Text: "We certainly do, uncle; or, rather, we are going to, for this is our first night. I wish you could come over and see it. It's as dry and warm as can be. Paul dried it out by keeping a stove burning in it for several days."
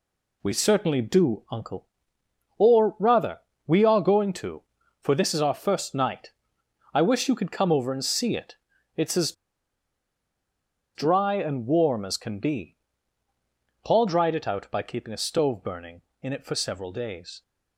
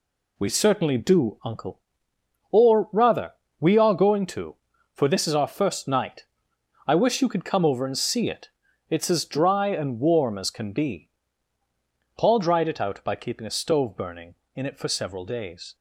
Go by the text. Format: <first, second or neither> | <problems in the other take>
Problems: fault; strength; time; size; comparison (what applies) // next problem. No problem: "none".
second | pauses between "as" and "dry"; strong; at 9.3 s; 1.6 s long